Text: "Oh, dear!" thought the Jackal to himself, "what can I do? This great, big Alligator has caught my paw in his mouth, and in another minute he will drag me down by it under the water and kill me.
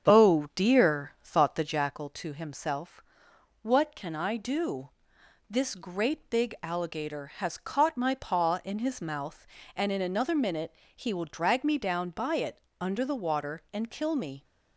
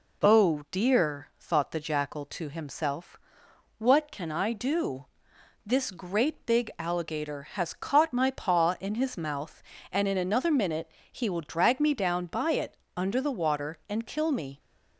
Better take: second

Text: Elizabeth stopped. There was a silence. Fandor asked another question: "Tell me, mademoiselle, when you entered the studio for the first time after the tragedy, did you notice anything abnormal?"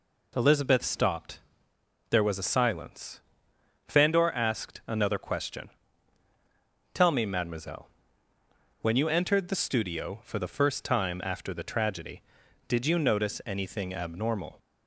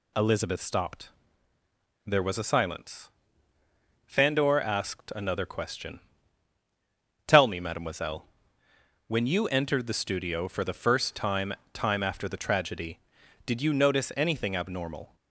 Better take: first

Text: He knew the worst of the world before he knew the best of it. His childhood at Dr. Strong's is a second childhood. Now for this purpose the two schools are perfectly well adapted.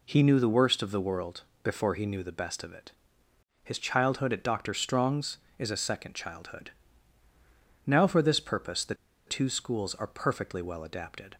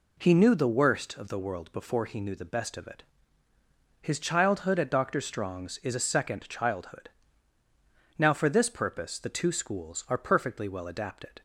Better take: second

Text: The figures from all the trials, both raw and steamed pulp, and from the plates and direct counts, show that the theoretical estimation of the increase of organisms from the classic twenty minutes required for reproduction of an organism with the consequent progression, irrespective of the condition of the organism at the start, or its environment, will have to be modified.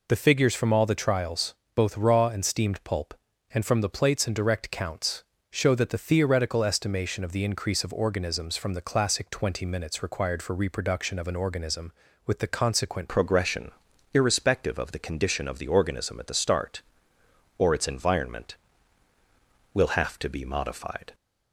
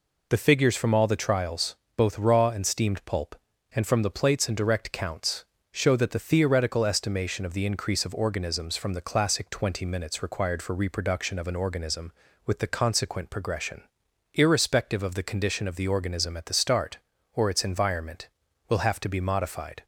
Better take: second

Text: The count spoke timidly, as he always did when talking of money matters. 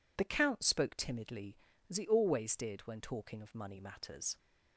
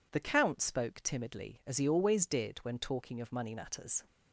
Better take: neither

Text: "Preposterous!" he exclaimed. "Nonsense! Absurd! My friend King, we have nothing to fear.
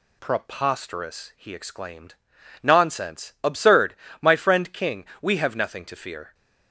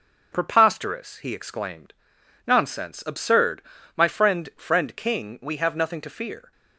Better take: first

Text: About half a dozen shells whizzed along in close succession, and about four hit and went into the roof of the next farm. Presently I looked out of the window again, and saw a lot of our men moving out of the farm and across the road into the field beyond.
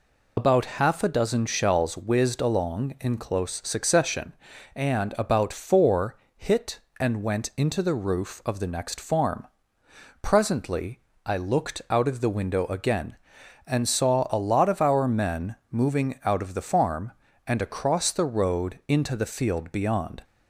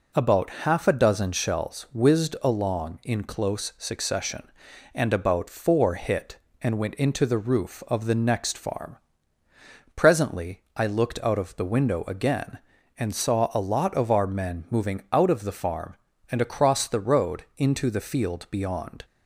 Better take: second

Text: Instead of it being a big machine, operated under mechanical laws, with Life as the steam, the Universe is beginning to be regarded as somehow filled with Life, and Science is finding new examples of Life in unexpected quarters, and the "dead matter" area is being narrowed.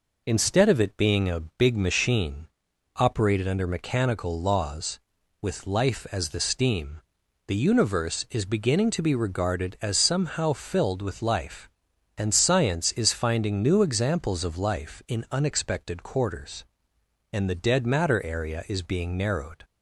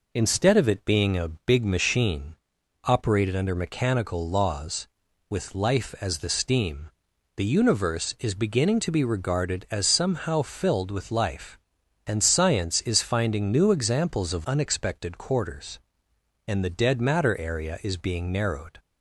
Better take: first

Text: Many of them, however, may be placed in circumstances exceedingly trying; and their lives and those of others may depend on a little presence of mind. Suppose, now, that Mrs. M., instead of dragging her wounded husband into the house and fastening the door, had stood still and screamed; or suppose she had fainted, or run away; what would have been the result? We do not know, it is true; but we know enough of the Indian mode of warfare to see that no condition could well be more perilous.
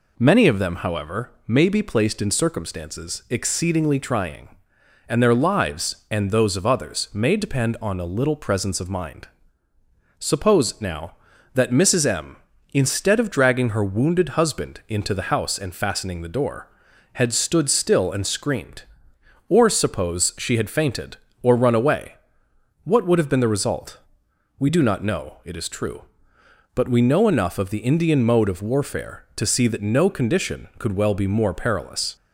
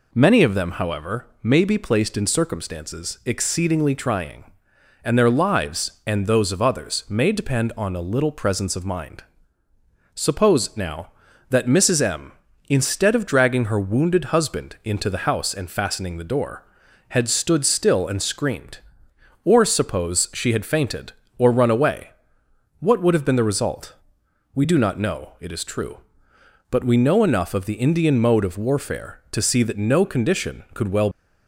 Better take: first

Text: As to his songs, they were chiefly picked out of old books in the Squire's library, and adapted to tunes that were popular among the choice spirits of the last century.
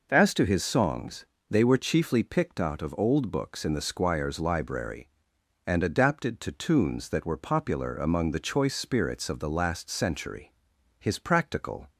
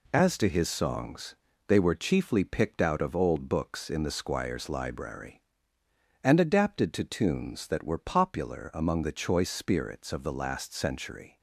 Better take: second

